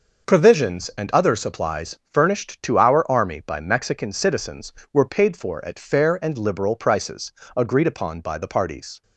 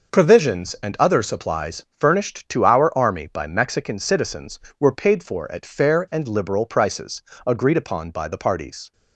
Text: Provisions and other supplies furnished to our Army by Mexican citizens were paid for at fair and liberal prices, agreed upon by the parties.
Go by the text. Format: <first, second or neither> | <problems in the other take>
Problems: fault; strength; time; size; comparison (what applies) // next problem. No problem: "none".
neither | pauses between "supplies" and "furnished"; slight; the same in both